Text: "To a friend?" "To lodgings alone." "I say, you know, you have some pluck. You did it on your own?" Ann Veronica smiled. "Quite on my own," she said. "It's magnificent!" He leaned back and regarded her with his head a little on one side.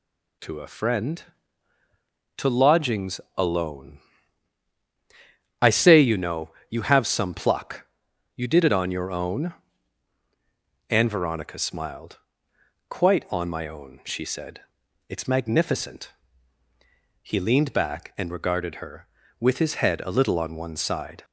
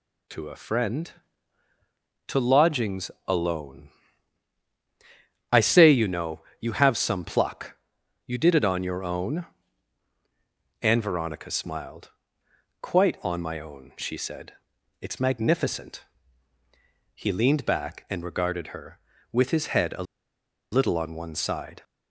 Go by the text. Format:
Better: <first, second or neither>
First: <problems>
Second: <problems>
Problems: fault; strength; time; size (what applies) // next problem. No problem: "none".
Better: first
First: pauses between "lodgings" and "alone"; slight; at 3.2 s; 0.16 s long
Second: pauses between "lodgings" and "alone"; slight; at 3.1 s; 0.16 s long // pauses between "a" and "little"; noticeable; at 20.0 s; 0.69 s long